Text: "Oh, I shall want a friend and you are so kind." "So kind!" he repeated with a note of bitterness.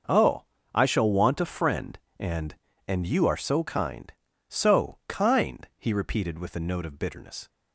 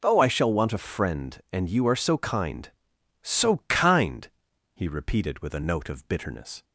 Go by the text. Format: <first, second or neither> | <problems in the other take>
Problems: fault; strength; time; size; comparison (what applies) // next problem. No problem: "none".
second | starts louder than the rest; noticeable; until 1.3 s; 6 dB // says "and" twice; at 2.8 s